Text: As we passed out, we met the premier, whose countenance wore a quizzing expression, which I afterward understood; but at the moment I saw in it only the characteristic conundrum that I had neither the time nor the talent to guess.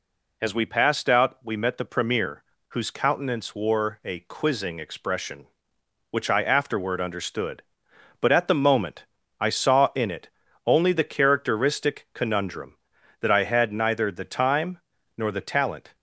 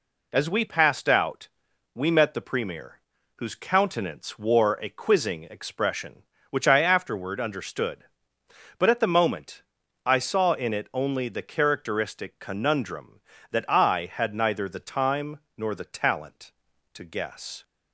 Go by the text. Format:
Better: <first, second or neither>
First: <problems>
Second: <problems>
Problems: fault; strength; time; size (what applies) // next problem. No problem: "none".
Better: second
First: pauses between "moment" and "I"; slight; at 9.0 s; 0.34 s long // pauses between "it" and "only"; slight; at 10.2 s; 0.34 s long // pauses between "time" and "nor"; at 14.7 s; 0.40 s long // stops before "to guess"; at 15.9 s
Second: pauses between "moment" and "I"; at 9.6 s; 0.42 s long // pauses between "time" and "nor"; slight; at 15.3 s; 0.18 s long